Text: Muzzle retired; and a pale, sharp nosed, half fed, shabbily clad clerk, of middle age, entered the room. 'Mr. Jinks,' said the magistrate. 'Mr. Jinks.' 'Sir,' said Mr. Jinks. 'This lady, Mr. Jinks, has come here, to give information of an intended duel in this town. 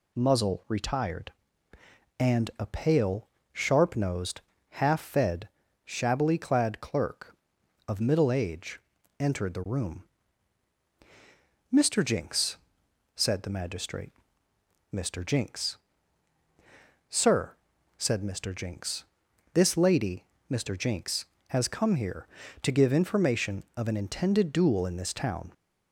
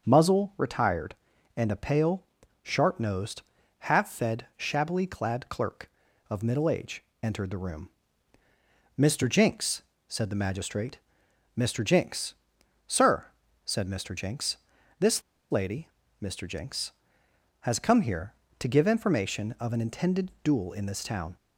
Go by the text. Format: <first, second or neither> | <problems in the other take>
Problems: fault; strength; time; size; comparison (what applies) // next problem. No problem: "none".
first | starts louder than the rest; until 1.1 s; 6.5 dB // pauses between "This" and "lady"; slight; at 15.2 s; 0.30 s long